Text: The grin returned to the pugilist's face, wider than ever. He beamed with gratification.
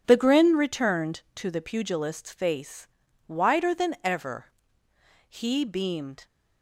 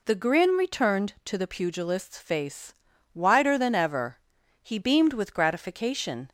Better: second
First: stops before "with gratification"; at 6.2 s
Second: none

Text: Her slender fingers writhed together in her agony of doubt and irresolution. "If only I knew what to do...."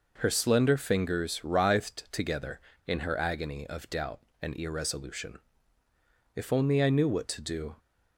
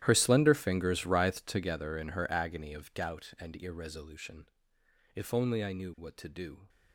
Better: first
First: none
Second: gets quieter; strong; throughout; 19 dB

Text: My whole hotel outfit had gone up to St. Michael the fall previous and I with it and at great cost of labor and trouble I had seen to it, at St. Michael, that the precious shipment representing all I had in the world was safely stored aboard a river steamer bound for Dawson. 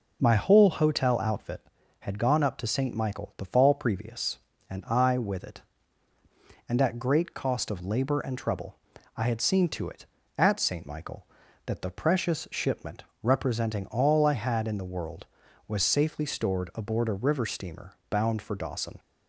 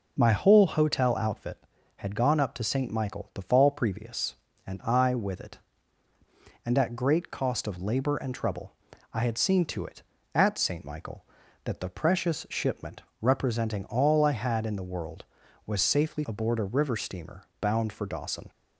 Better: first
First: pauses between "trouble" and "I"; at 8.7 s; 0.40 s long // pauses between "shipment" and "representing"; slight; at 13.0 s; 0.20 s long // pauses between "steamer" and "bound"; slight; at 17.9 s; 0.16 s long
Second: pauses between "trouble" and "I"; at 8.7 s; 0.40 s long // pauses between "shipment" and "representing"; slight; at 13.0 s; 0.20 s long // skips "stored"; at 16.2 s // pauses between "steamer" and "bound"; slight; at 17.4 s; 0.16 s long

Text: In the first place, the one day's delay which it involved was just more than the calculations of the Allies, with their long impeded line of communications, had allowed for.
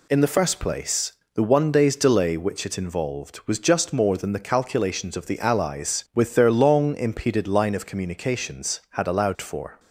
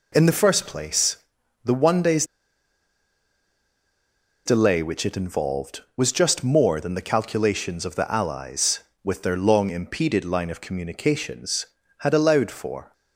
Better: first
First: none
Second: pauses between "day's" and "delay"; strong; at 2.2 s; 2.2 s long

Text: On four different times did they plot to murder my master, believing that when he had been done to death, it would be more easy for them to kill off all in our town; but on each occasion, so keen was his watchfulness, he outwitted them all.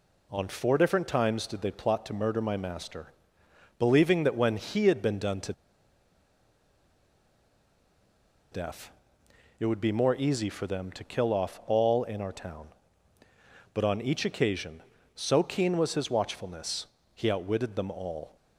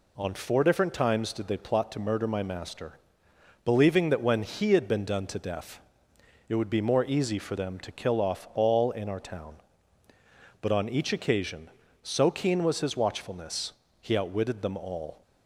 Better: second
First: pauses between "to" and "death"; strong; at 5.5 s; 2.9 s long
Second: none

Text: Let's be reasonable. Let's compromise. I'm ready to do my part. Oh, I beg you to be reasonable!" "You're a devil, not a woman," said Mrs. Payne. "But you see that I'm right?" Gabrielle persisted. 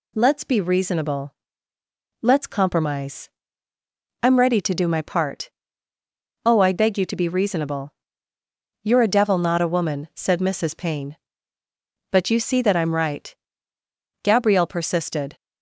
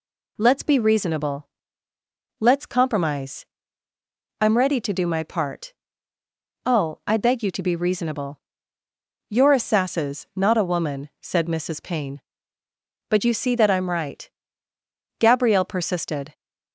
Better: first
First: none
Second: says "sasses" for "devil"; at 9.6 s

